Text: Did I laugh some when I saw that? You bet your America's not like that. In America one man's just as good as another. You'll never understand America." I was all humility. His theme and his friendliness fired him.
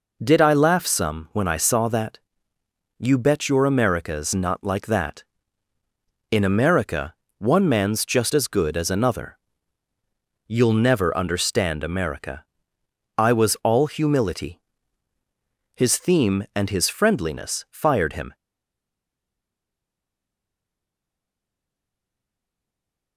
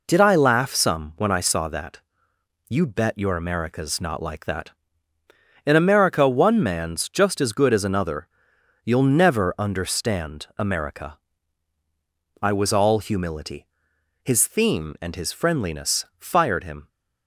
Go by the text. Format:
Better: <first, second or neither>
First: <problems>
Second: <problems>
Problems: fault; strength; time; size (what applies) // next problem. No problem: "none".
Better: second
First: pauses between "America" and "one"; slight; at 7.1 s; 0.26 s long // stays silent after the last word; strong; from 18.3 s on; 4.8 s long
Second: none